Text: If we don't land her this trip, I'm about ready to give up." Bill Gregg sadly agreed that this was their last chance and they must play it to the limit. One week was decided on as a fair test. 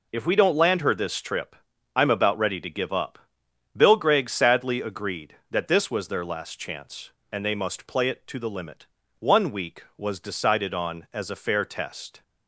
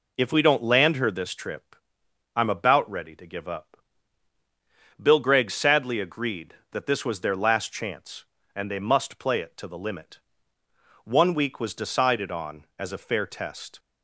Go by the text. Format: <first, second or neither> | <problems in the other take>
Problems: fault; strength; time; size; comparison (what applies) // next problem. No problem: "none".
neither | none